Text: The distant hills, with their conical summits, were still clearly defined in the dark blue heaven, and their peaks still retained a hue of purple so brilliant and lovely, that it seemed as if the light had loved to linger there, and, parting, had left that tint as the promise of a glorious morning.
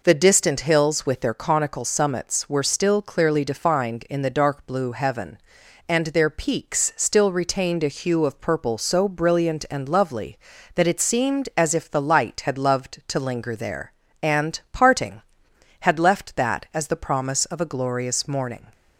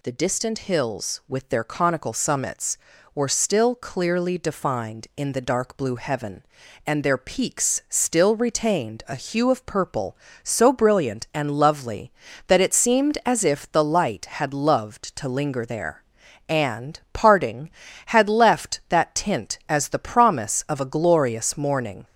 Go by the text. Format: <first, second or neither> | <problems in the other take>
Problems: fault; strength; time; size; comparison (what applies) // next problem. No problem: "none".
second | skips "tint"; at 16.7 s